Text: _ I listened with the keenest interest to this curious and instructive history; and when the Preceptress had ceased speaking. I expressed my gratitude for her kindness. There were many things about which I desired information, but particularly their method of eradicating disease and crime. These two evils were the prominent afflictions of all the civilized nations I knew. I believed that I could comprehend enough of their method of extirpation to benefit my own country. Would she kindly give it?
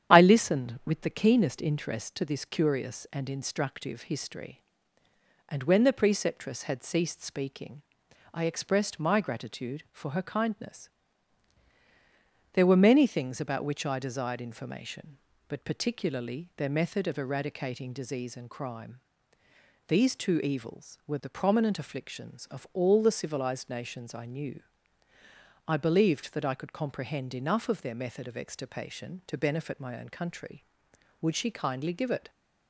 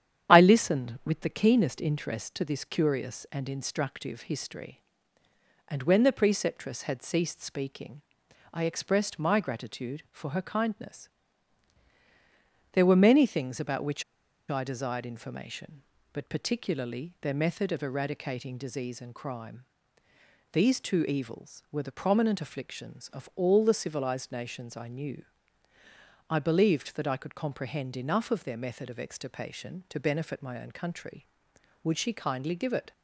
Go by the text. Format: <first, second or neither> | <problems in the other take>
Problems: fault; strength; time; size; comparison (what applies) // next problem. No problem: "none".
first | starts louder than the rest; strong; until 1.3 s; 9.5 dB; strong in the first // pauses between "which" and "I"; noticeable; at 14.0 s; 0.46 s long